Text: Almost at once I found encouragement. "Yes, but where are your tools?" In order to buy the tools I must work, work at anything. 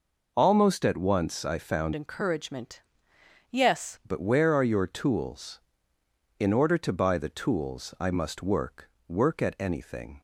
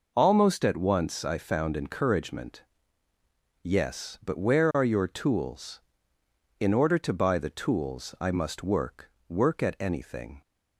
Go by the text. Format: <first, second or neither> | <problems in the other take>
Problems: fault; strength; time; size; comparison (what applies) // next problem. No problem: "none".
second | changes voice from "encouragement" to "Yes"; from 1.9 to 3.9 s; 2.0 s long